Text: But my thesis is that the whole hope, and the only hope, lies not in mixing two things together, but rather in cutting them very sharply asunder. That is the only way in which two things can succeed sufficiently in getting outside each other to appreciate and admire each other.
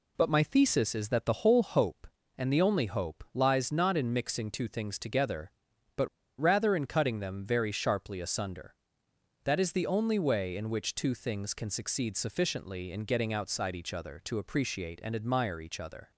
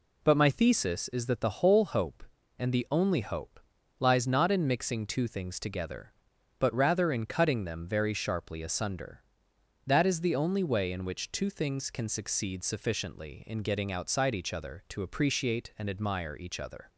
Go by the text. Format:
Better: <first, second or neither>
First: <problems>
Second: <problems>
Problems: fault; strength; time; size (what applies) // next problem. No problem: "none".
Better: second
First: pauses between "but" and "rather"; slight; at 6.0 s; 0.32 s long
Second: none